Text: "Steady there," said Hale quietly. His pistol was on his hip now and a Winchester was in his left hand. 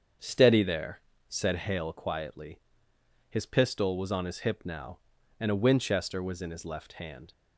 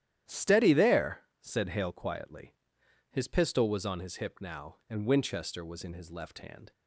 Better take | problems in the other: first | starts louder than the rest; strong; until 1.4 s; 11.5 dB; strong in the first // skips "a"; at 5.0 s

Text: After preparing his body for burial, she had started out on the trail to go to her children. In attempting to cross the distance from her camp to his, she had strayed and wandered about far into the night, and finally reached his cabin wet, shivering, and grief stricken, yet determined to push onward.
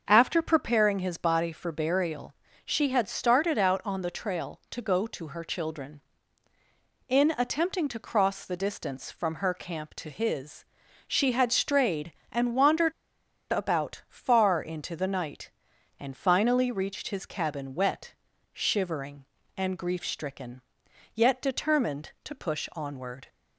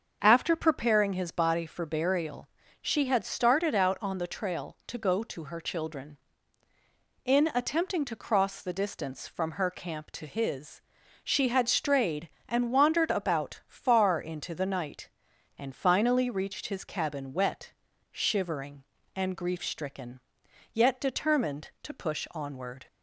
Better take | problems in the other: second | starts louder than the rest; until 1.0 s; 6.5 dB; also in the second // pauses between "wandered" and "about"; noticeable; at 12.9 s; 0.59 s long

